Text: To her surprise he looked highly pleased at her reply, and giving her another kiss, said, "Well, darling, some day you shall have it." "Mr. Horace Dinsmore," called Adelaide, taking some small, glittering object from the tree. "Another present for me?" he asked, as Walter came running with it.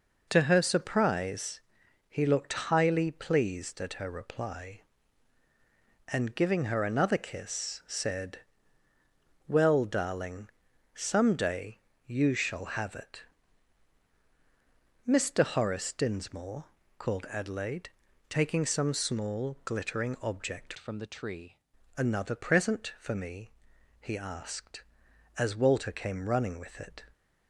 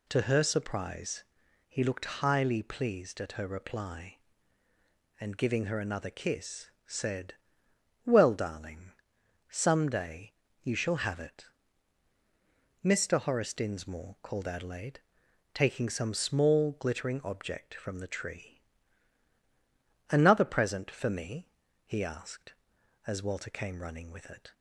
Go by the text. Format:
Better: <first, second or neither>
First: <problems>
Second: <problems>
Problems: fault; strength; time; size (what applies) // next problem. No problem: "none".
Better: second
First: pauses between "surprise" and "he"; noticeable; at 1.5 s; 0.50 s long // pauses between "day" and "you"; slight; at 11.7 s; 0.26 s long // changes voice from "from" to "tree"; from 20.7 to 21.5 s; 0.8 s long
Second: pauses between "surprise" and "he"; at 1.2 s; 0.44 s long // pauses between "day" and "you"; slight; at 10.3 s; 0.30 s long